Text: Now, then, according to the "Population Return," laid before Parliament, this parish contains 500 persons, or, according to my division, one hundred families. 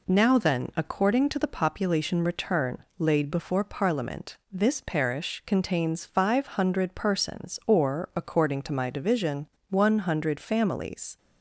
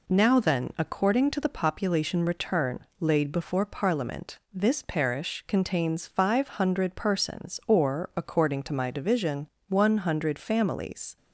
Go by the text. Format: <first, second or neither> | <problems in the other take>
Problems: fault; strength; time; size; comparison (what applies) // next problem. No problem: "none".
neither | none